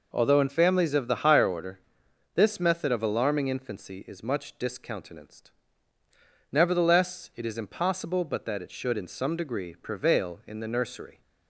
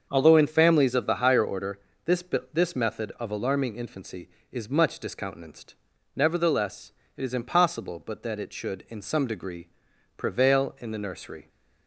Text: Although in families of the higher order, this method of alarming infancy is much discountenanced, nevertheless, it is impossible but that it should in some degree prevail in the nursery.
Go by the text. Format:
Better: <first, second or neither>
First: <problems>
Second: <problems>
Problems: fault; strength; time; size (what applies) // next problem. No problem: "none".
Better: first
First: none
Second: starts louder than the rest; until 1.1 s; 7 dB // says "this" twice; at 2.5 s // pauses between "degree" and "prevail"; noticeable; at 9.6 s; 0.48 s long